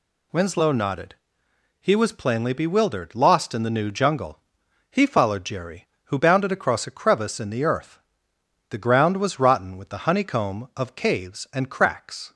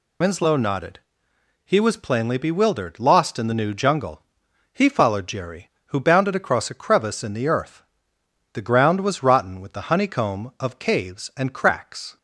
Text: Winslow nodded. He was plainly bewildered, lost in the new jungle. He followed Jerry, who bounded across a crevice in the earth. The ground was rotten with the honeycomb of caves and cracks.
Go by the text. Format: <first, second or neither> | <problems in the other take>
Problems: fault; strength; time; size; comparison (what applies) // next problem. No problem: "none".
first | loses the start of "Winslow"; at 0.2 s; 45 ms